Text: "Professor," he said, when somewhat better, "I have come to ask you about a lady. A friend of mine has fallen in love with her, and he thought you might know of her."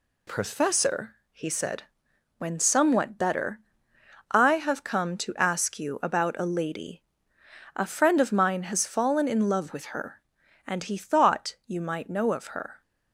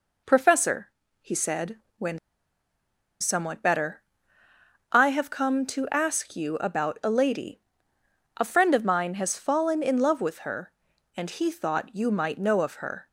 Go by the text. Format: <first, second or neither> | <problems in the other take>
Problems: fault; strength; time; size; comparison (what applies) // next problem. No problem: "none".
first | pauses between "when" and "somewhat"; at 2.1 s; 1.0 s long